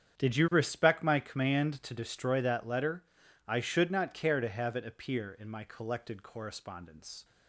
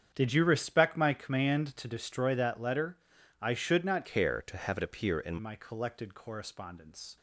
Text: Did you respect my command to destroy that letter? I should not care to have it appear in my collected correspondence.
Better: first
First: starts louder than the rest; strong; until 1.2 s; 8.5 dB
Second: starts louder than the rest; strong; until 1.1 s; 8 dB // changes voice from "care" to "in"; from 4.0 to 5.3 s; 1.3 s long

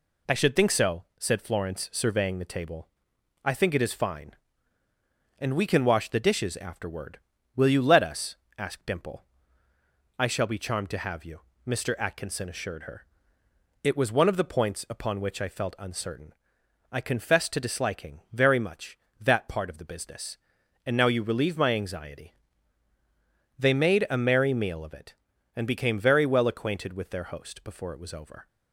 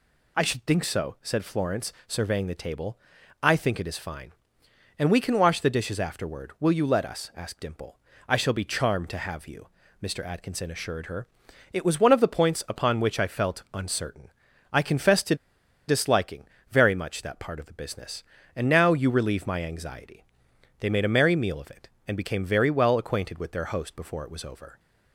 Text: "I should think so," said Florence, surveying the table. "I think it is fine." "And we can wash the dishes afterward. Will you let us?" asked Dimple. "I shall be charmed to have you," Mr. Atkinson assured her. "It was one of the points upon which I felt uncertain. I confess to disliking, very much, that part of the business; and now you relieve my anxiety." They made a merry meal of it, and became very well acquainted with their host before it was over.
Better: first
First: none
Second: pauses between "to" and "disliking"; noticeable; at 15.3 s; 0.53 s long

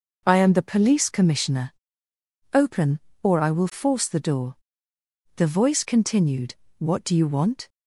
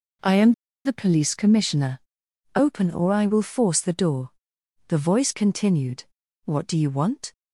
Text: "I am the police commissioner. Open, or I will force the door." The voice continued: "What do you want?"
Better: first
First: none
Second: pauses between "am" and "the"; slight; at 0.5 s; 0.33 s long

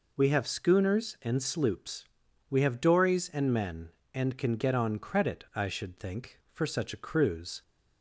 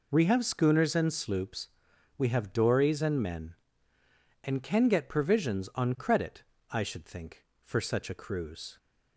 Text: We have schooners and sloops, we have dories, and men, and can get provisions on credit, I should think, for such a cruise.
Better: second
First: skips "provisions"; at 4.7 s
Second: none

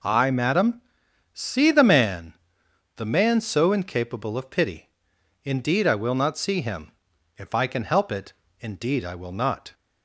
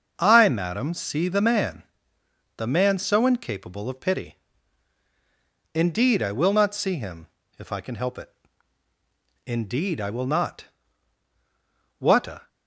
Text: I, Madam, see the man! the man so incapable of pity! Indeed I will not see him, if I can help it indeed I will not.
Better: first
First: pauses between "it" and "indeed"; slight; at 8.3 s; 0.30 s long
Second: starts louder than the rest; until 1.1 s; 6.5 dB // pauses between "it" and "indeed"; at 8.2 s; 1.1 s long // goes on to say "What a"; slight; from 11.9 s on; 0.48 s long

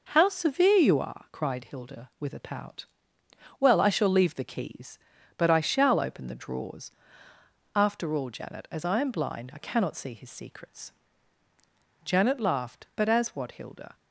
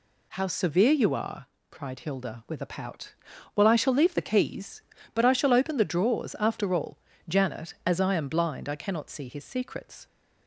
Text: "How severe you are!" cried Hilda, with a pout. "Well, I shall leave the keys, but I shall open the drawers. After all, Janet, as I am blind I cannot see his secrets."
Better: second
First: goes on to say "Janet laughed but as what Hilda"; strong; from 12.0 s on; 1.9 s long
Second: none

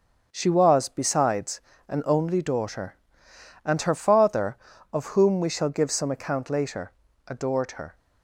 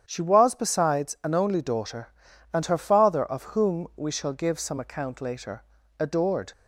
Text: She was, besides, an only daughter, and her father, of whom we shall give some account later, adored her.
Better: first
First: starts louder than the rest; until 1.3 s; 6.5 dB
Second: starts louder than the rest; strong; until 1.0 s; 9 dB // stops before "her"; at 6.5 s

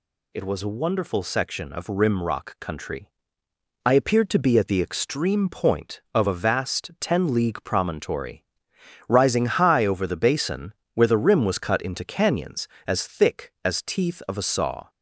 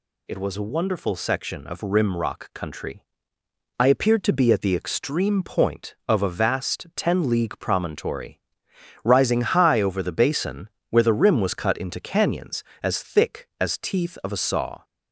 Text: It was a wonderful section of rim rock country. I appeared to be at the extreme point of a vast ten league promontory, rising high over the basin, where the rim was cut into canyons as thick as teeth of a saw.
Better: neither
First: none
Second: none

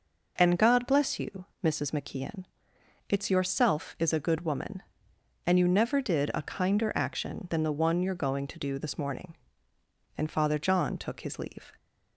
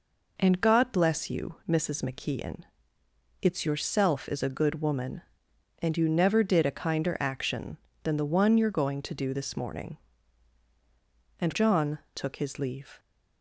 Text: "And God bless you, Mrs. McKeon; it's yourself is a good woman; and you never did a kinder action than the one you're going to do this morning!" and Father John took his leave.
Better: first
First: none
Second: skips "Father"; at 11.5 s // pauses between "John" and "took"; slight; at 11.9 s; 0.16 s long

